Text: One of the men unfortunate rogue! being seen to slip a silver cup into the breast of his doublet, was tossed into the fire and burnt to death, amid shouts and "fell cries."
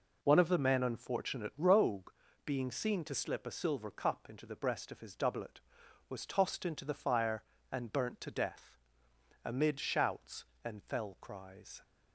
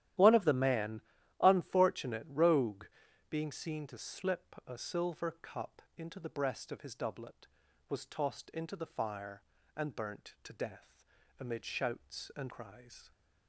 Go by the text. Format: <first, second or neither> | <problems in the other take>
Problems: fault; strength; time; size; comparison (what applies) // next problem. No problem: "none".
first | starts louder than the rest; strong; until 1.5 s; 12.5 dB // pauses between "men" and "unfortunate"; at 0.9 s; 0.40 s long // pauses between "cup" and "into"; slight; at 5.7 s; 0.16 s long // skips "fell"; at 12.5 s